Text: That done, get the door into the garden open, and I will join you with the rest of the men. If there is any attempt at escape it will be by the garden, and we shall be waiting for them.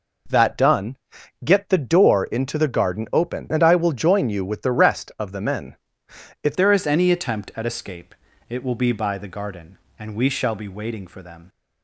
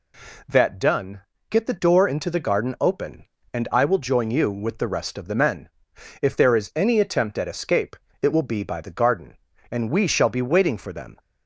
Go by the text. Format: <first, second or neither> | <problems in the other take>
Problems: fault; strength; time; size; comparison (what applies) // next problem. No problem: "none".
second | changes voice at "there"; from 6.5 s on; 4.9 s long // pauses between "escape" and "it"; slight; at 8.1 s; 0.34 s long; slight in the second